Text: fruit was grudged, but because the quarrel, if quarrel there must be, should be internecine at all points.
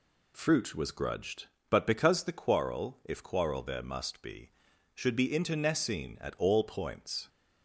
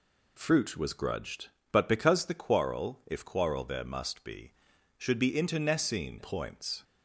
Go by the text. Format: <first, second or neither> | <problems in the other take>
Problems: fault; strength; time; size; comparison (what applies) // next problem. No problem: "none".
first | skips "at all"; at 6.2 s